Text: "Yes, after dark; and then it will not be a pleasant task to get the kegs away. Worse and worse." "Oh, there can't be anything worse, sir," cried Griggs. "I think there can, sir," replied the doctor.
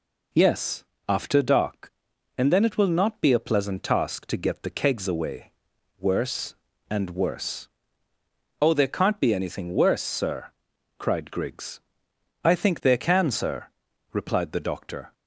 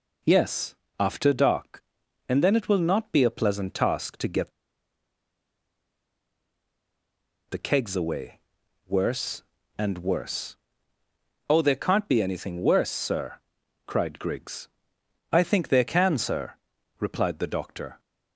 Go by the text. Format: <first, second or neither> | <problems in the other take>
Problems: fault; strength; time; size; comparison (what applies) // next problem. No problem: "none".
first | pauses between "get" and "the"; strong; at 4.5 s; 2.9 s long